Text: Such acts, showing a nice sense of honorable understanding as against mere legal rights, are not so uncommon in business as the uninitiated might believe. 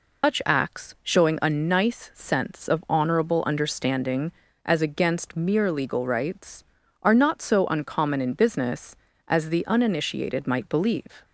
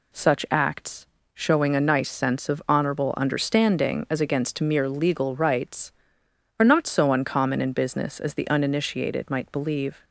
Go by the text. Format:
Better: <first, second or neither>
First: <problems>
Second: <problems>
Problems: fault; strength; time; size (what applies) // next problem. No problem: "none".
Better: second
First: loses the start of "Such"; at 0.2 s; 160 ms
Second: none